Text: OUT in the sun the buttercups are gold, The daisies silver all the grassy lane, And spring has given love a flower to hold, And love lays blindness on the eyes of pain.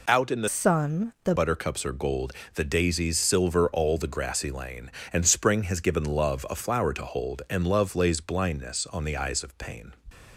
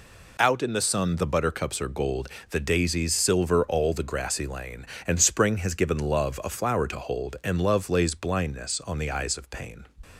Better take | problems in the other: second | changes voice from "sun" to "the"; from 0.4 to 1.3 s; 0.9 s long

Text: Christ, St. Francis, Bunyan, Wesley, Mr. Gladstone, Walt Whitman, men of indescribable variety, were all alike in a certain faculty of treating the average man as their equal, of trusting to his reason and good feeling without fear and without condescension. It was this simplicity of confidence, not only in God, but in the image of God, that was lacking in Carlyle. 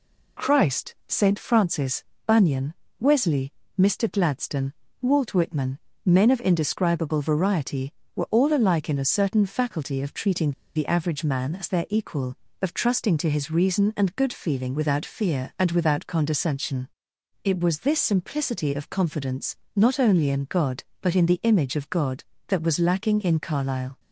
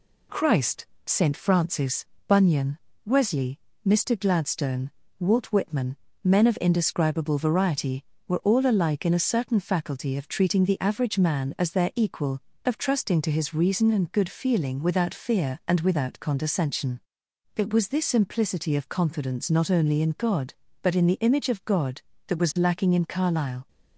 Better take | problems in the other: second | pauses between "treating" and "the"; slight; at 10.5 s; 0.23 s long

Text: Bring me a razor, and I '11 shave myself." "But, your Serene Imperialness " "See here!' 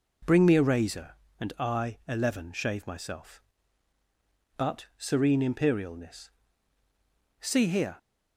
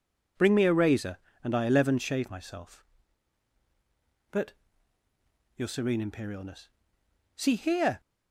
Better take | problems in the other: second | skips "your"; at 4.9 s

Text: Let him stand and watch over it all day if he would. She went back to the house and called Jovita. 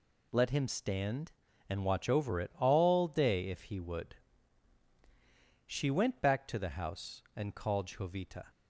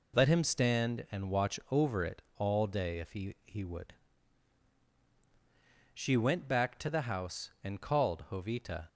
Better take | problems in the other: first | pauses between "it" and "all"; slight; at 2.2 s; 0.16 s long // says "he" twice; at 3.4 s

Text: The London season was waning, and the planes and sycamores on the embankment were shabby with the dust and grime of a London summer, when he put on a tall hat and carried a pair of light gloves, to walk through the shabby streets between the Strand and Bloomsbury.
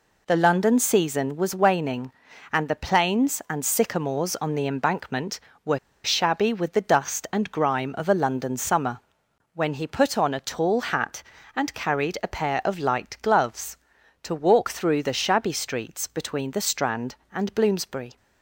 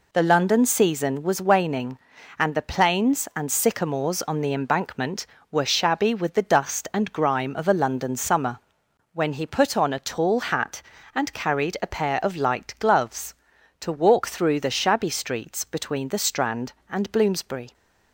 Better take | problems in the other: second | pauses between "were" and "shabby"; slight; at 5.7 s; 0.25 s long

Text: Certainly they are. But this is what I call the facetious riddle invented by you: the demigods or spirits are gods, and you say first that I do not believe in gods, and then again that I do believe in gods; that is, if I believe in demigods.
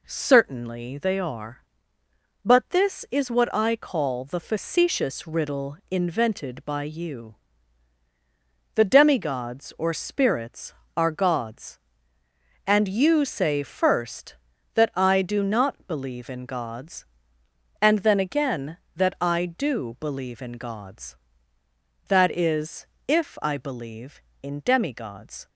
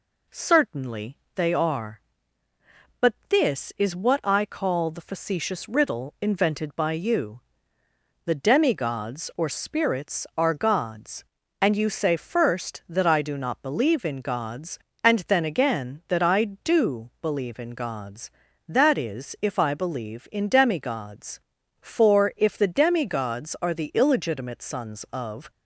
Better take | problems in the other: first | pauses between "Certainly" and "they"; slight; at 1.1 s; 0.18 s long // goes on to say "For if the demigods are the illegitimate sons of"; strong; from 21.7 s on; 3.7 s long

